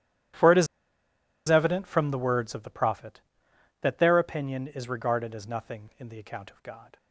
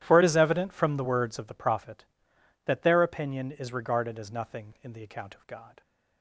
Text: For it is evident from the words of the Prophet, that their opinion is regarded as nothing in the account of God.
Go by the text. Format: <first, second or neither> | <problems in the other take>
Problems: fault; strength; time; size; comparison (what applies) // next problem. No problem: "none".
second | starts louder than the rest; strong; until 2.1 s; 12 dB; strong in the second // pauses between "is" and "evident"; noticeable; at 0.6 s; 0.82 s long